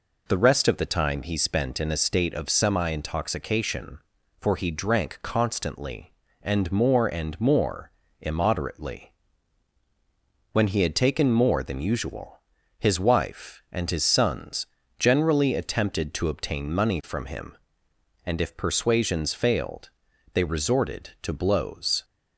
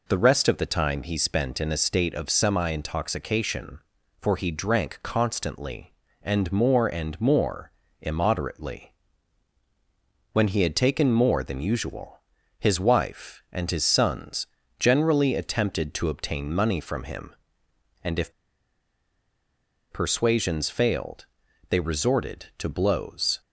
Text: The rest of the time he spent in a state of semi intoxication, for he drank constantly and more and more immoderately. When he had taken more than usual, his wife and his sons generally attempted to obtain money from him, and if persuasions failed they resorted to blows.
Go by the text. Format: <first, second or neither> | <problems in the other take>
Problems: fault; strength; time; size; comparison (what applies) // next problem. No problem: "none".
first | pauses between "more" and "immoderately"; slight; at 7.7 s; 0.28 s long; slight in the first // pauses between "sons" and "generally"; slight; at 14.4 s; 0.32 s long; slight in the first // pauses between "if" and "persuasions"; strong; at 18.3 s; 1.5 s long // pauses between "failed" and "they"; noticeable; at 21.2 s; 0.46 s long; noticeable in the first